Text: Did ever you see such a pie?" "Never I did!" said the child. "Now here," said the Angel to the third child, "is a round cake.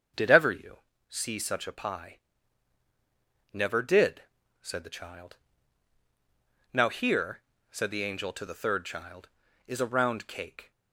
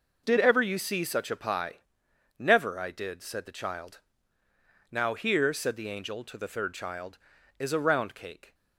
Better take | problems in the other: second | starts louder than the rest; until 1.4 s; 6.5 dB // pauses between "you" and "see"; slight; at 0.7 s; 0.32 s long // skips "I"; at 3.8 s

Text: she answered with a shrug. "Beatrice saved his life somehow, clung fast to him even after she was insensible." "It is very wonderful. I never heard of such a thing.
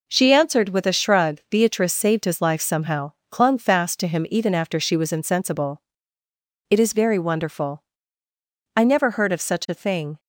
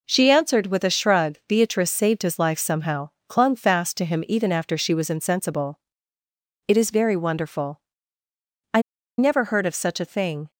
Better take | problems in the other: first | pauses between "I" and "never"; at 8.8 s; 0.36 s long

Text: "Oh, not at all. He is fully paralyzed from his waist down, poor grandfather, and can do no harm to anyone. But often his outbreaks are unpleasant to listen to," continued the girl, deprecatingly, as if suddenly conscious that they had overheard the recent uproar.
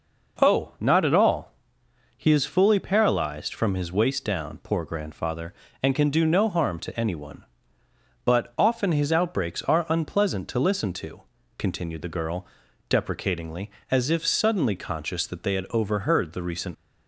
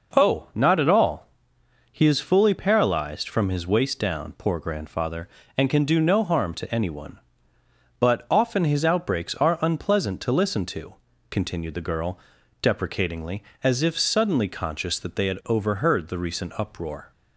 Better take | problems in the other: second | stops before "uproar"; at 16.7 s

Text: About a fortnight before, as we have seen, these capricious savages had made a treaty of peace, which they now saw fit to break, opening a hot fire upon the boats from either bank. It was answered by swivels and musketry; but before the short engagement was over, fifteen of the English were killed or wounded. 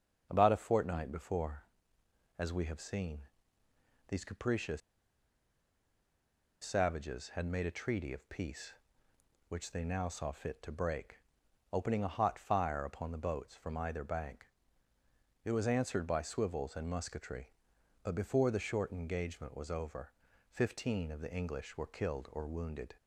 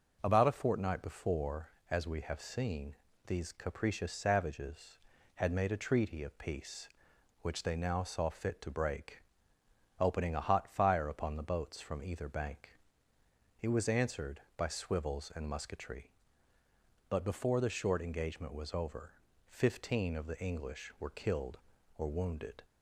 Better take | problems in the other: second | starts louder than the rest; until 1.3 s; 6.5 dB // pauses between "capricious" and "savages"; strong; at 4.8 s; 1.8 s long

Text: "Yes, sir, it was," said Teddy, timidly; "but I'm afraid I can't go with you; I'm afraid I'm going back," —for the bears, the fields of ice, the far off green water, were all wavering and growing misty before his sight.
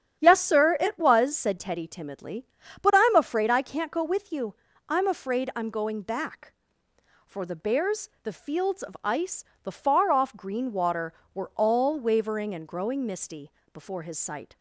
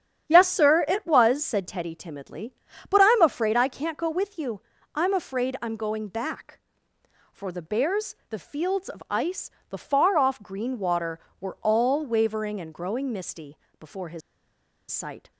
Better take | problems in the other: first | starts louder than the rest; strong; until 1.3 s; 9.5 dB; strong in the first // pauses between "misty" and "before"; slight; at 13.5 s; 0.22 s long; slight in the first // pauses between "his" and "sight"; noticeable; at 14.2 s; 0.70 s long

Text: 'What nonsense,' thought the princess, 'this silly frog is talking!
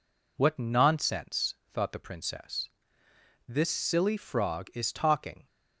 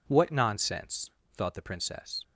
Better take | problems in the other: first | stops before "this silly frog is talking"; at 2.2 s

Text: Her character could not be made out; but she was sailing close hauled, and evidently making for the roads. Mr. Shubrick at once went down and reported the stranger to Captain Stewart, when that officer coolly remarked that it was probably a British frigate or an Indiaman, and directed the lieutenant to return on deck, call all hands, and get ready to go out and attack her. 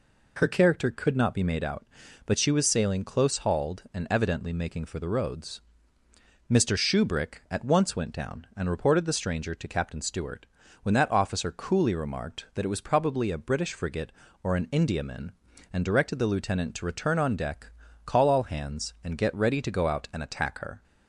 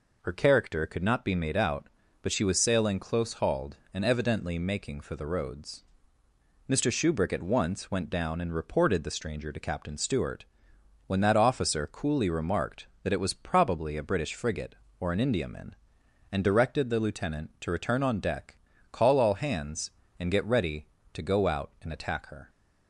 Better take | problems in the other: neither | none

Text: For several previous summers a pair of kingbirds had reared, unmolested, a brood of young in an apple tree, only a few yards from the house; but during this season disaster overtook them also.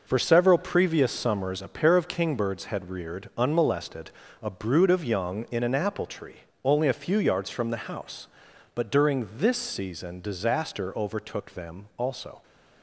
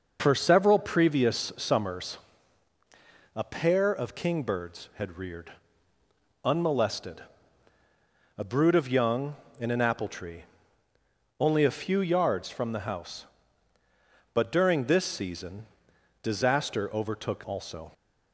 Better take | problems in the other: first | pauses between "summers" and "a"; at 2.1 s; 1.1 s long // pauses between "season" and "disaster"; noticeable; at 15.6 s; 0.56 s long // skips "them"; at 17.4 s

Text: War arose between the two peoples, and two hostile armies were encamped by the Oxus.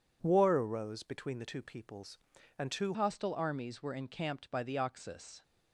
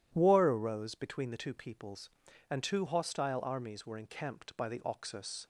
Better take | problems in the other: second | changes voice at "hostile"; from 2.9 s on; 2.5 s long

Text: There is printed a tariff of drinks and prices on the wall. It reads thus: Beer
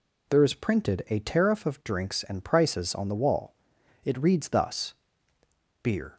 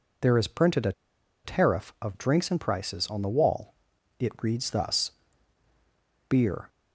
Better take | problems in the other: first | pauses between "a" and "tariff"; noticeable; at 0.9 s; 0.52 s long

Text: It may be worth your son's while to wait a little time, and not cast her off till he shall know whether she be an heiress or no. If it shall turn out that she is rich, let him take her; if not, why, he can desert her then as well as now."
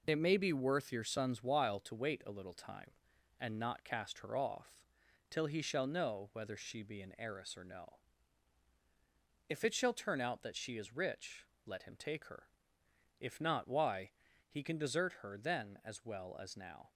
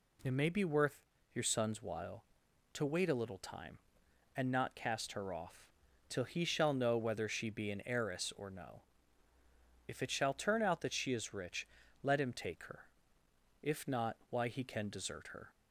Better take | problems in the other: first | pauses between "worth" and "your"; slight; at 0.9 s; 0.36 s long // pauses between "off" and "till"; at 5.6 s; 0.44 s long; noticeable in the first // stops before "then as well as now"; at 15.5 s

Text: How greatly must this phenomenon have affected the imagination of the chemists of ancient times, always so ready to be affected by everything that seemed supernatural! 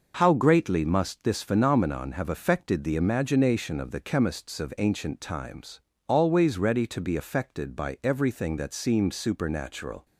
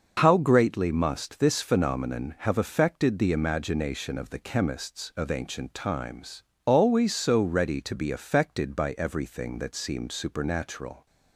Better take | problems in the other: second | skips "so"; at 6.5 s

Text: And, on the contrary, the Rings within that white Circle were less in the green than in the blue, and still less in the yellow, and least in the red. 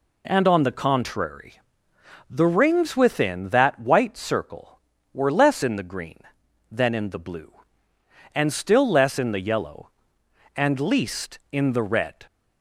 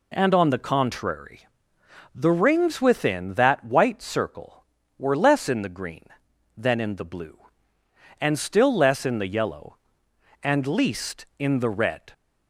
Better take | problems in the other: neither | none

